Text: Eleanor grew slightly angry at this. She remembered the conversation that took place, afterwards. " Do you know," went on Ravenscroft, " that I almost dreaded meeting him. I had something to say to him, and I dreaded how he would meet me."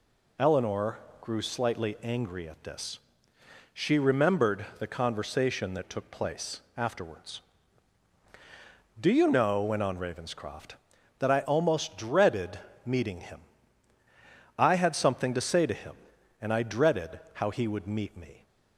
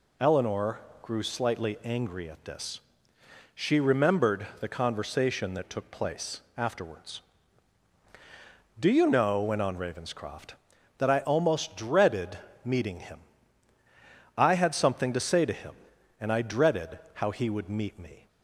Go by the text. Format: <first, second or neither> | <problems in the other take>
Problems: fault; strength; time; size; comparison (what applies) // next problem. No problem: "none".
neither | pauses between "Eleanor" and "grew"; slight; the same in both // pauses between "dreaded" and "meeting"; slight; the same in both